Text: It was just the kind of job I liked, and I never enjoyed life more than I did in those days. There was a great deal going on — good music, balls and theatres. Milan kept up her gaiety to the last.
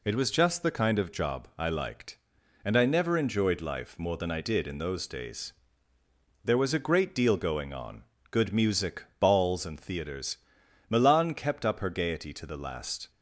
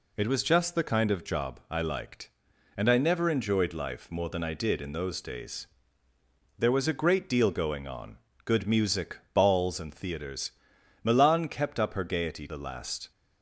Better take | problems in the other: first | skips "to"; at 12.4 s

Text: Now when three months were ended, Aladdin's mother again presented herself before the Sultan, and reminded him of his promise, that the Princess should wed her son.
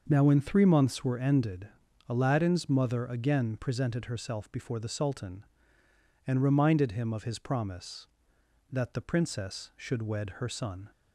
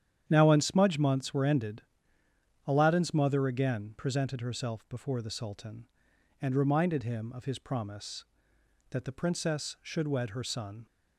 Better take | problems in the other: first | starts louder than the rest; strong; until 1.2 s; 9.5 dB; noticeable in the first // says "smudge" for "three"; at 0.5 s

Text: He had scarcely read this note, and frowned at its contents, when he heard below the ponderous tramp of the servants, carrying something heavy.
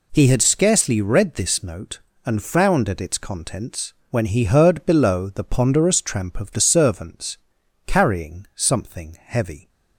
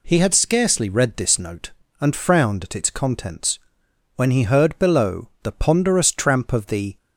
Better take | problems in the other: first | stops before "servants carrying something heavy"; at 6.9 s

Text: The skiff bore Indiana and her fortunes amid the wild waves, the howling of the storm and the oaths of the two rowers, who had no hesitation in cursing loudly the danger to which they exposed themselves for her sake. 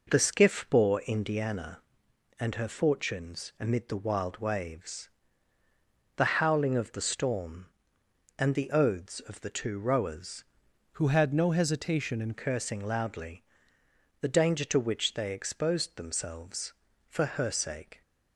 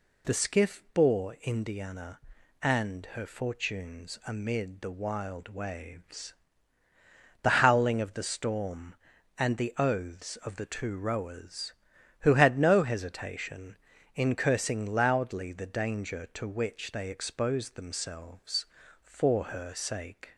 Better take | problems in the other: second | changes voice from "who" to "in"; from 10.9 to 12.3 s; 1.4 s long // pauses between "loudly" and "the"; noticeable; at 13.4 s; 0.78 s long

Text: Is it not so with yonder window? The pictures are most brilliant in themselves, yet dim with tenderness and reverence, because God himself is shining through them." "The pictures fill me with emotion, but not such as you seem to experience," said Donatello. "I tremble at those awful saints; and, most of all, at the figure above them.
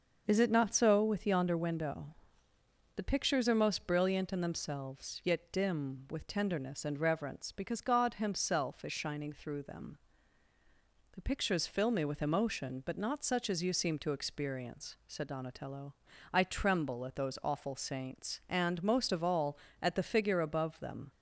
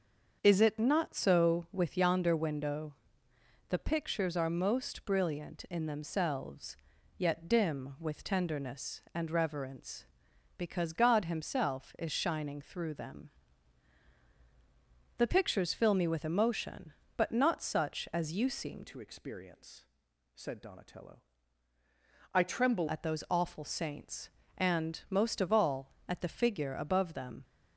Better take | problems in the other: first | starts louder than the rest; until 1.4 s; 6.5 dB; noticeable in the first // changes voice from "to" to "tremble"; from 18.8 to 22.8 s; 4.0 s long

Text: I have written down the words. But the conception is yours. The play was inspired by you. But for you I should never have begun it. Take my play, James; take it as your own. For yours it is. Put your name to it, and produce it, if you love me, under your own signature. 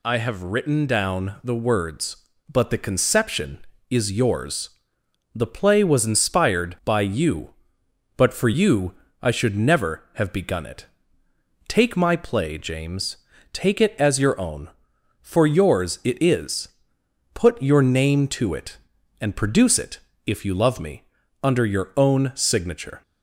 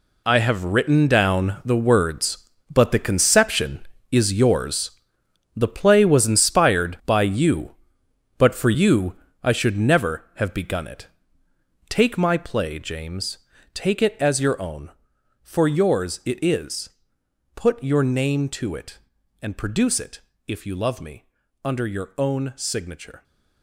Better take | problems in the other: first | gets quieter; strong; throughout; 12 dB // pauses between "you" and "I"; slight; at 9.1 s; 0.28 s long; slight in the first

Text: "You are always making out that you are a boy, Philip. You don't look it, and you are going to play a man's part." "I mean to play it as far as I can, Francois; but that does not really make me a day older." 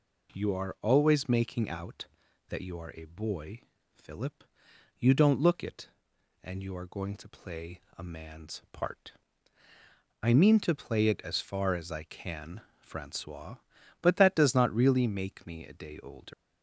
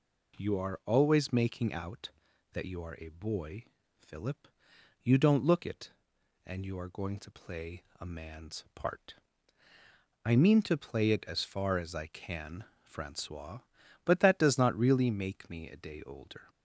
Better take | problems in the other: second | pauses between "play" and "a"; slight; at 7.8 s; 0.16 s long; slight in the second // leaves "older" unfinished; at 16.3 s; 120 ms

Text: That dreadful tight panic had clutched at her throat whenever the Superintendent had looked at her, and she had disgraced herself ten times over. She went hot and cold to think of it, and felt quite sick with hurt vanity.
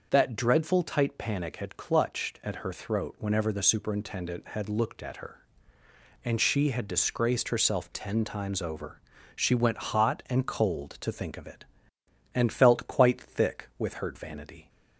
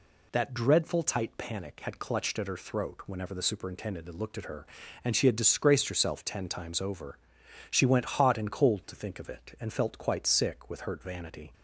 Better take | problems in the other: second | starts louder than the rest; noticeable; until 1.1 s; 6 dB // says "thick" for "sick"; at 13.1 s

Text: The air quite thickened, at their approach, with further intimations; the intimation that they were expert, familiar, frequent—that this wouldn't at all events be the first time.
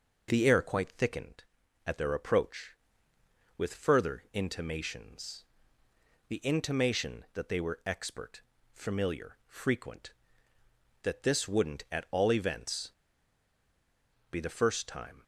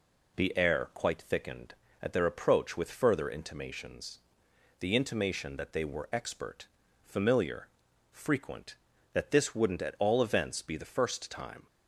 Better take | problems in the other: second | pauses between "events" and "be"; strong; at 12.9 s; 1.3 s long

